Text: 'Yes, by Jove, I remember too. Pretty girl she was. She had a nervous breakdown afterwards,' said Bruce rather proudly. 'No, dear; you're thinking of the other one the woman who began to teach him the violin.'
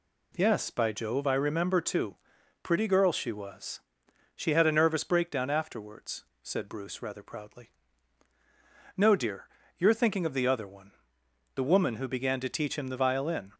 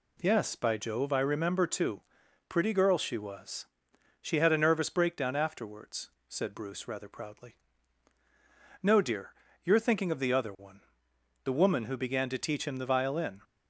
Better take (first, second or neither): neither